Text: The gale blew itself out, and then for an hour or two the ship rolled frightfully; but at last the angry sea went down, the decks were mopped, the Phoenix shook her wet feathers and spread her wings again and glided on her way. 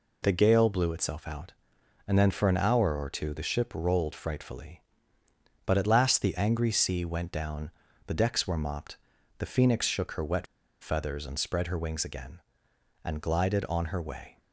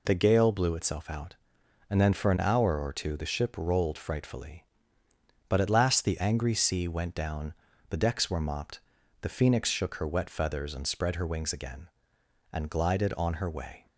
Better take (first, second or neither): second